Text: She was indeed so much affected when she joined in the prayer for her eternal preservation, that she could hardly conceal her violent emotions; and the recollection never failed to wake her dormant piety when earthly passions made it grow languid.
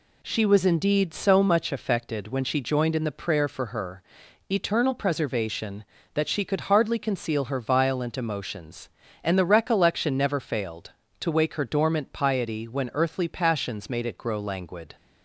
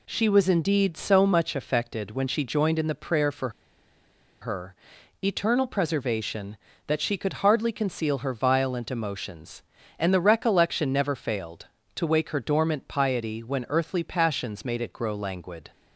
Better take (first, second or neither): first